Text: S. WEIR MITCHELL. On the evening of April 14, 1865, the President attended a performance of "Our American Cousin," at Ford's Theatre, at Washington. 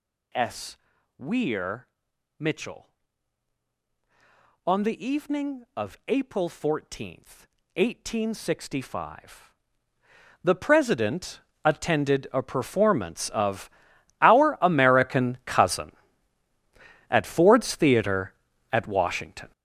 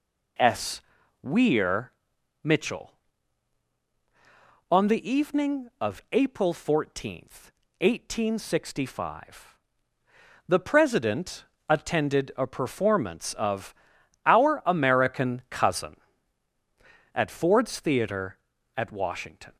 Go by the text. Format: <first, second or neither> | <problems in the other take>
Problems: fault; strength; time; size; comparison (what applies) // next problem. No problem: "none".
second | gets louder; strong; throughout; 10.5 dB // pauses between "WEIR" and "MITCHELL"; noticeable; at 1.8 s; 0.52 s long; noticeable in the second // pauses between "President" and "attended"; slight; at 11.3 s; 0.24 s long; slight in the second // pauses between "of" and "Our"; noticeable; at 13.6 s; 0.52 s long; noticeable in the second